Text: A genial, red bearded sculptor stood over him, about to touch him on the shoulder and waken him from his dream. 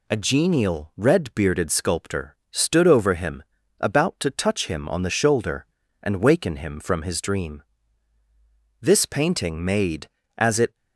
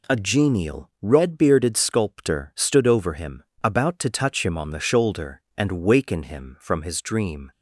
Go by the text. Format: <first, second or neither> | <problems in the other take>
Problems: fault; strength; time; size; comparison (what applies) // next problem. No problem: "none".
second | pauses between "sculptor" and "stood"; slight; at 2.3 s; 0.16 s long // goes on to say "This painting made as it"; strong; from 8.8 s on; 1.9 s long